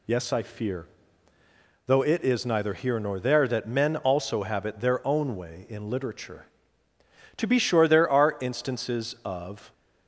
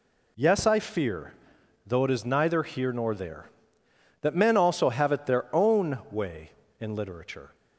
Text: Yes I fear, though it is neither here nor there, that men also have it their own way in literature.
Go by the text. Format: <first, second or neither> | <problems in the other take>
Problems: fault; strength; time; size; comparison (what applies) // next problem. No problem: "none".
second | goes on to say "To be sure there are instances of"; strong; from 7.3 s on; 2.3 s long